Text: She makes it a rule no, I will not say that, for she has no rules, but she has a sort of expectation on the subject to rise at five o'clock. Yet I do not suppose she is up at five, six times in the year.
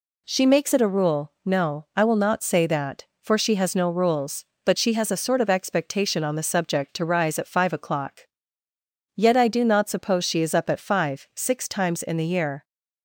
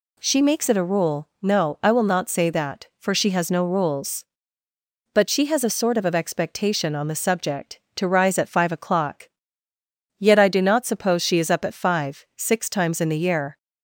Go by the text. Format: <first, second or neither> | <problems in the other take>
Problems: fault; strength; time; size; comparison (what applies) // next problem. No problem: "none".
first | says "of" twice; at 6.0 s